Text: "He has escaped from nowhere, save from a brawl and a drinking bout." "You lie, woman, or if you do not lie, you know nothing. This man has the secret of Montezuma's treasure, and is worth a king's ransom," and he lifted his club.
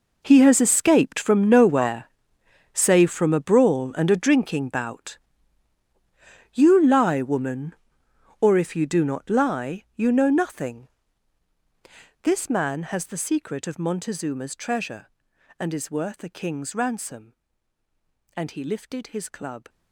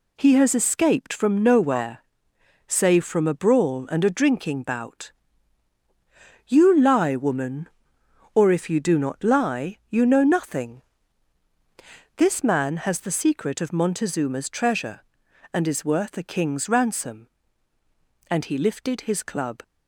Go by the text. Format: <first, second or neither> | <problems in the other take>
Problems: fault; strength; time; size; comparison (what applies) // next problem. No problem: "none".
second | gets quieter; strong; throughout; 15.5 dB